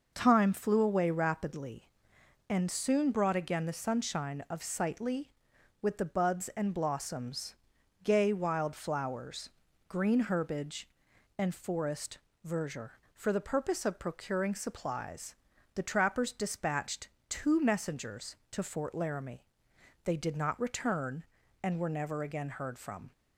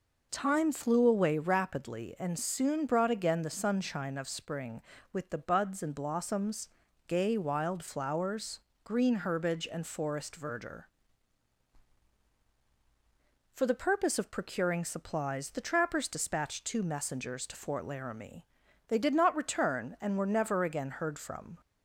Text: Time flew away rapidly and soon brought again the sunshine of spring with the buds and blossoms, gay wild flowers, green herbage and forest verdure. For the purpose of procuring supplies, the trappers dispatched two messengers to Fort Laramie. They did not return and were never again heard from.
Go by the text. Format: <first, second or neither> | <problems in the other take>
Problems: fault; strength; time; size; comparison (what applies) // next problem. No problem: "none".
second | says "sightly" for "spring"; at 4.6 s // pauses between "forest" and "verdure"; slight; at 12.1 s; 0.26 s long // pauses between "dispatched" and "two"; slight; at 17.0 s; 0.20 s long